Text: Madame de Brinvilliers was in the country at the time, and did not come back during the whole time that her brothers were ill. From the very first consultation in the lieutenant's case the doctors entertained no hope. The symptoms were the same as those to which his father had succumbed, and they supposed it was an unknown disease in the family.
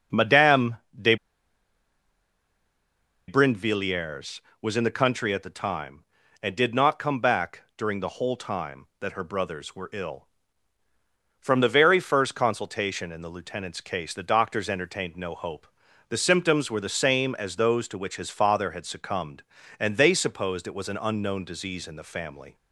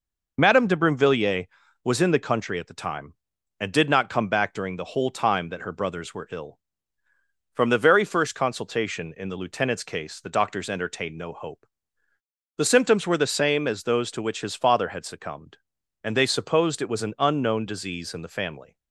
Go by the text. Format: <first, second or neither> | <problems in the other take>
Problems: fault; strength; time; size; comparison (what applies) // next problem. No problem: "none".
second | starts louder than the rest; noticeable; until 3.5 s; 6 dB // pauses between "Madame" and "de"; slight; at 0.7 s; 0.24 s long // pauses between "de" and "Brinvilliers"; strong; at 1.1 s; 2.1 s long